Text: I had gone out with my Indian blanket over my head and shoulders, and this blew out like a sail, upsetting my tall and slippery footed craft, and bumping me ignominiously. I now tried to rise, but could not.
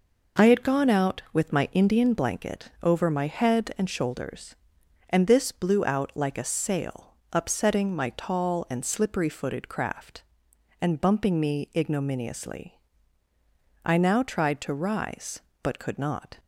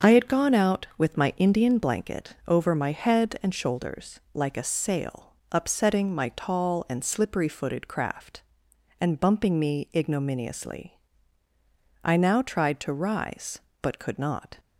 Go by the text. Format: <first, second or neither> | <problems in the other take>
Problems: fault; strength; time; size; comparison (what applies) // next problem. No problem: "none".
first | starts louder than the rest; until 1.1 s; 6.5 dB // skips "and this blew out"; at 4.2 s